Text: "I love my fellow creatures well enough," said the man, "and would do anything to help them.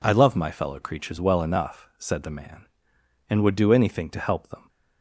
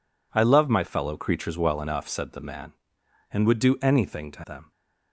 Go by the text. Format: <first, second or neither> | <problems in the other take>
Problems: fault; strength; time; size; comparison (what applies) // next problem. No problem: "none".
first | skips "help"; at 4.4 s